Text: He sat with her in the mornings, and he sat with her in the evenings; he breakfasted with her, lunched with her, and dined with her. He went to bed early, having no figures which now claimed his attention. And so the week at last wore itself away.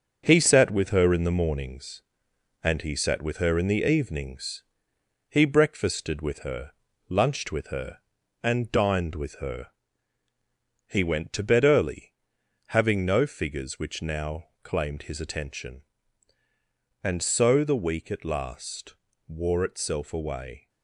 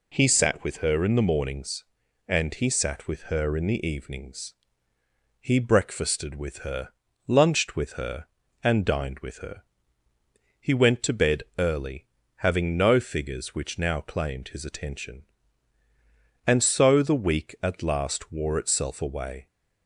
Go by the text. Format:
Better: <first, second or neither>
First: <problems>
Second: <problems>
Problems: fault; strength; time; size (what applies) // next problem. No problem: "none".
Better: second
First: gets quieter; throughout; 6.5 dB // pauses between "now" and "claimed"; slight; at 14.4 s; 0.16 s long // pauses between "last" and "wore"; slight; at 18.9 s; 0.34 s long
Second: none